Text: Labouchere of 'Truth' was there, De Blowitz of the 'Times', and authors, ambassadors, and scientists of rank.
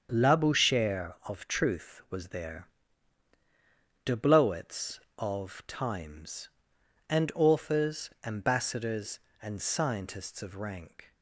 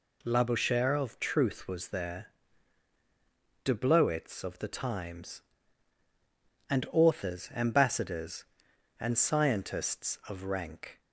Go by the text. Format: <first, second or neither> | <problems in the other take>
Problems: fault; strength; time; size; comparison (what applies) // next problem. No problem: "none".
second | starts louder than the rest; strong; until 1.1 s; 7 dB // skips "the"; at 5.6 s